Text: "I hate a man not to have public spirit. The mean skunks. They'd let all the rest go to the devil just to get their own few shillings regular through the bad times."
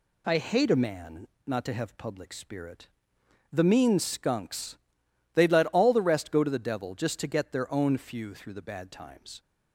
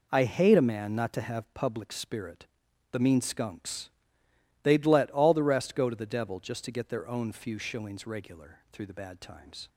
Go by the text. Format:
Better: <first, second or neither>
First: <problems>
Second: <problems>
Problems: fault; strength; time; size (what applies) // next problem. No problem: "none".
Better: second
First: pauses between "man" and "not"; slight; at 1.2 s; 0.19 s long // skips "shillings regular"; at 8.3 s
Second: none